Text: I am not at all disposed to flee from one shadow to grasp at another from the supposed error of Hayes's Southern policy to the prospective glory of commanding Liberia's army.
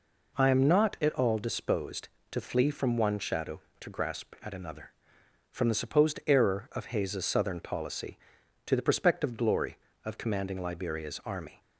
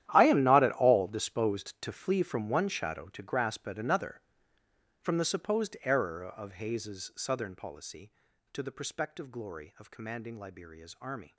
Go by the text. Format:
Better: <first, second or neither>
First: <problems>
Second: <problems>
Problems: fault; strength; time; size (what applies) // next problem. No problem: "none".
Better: first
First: none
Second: gets quieter; strong; throughout; 16 dB